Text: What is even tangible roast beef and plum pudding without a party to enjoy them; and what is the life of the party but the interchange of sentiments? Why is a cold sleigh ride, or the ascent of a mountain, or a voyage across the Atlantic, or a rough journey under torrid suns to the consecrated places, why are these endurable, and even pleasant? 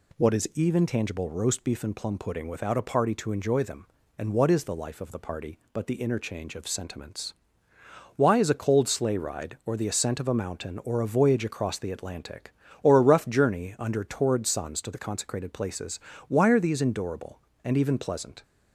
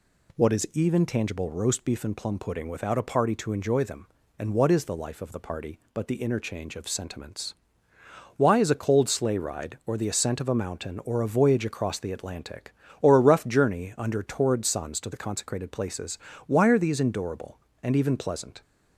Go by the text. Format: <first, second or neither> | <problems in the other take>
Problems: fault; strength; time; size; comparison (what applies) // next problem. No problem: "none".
neither | none